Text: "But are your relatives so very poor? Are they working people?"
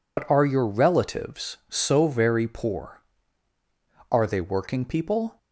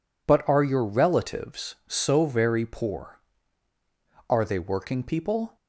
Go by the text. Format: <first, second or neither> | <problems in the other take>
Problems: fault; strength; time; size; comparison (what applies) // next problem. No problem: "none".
second | loses the start of "But"; at 0.1 s; 95 ms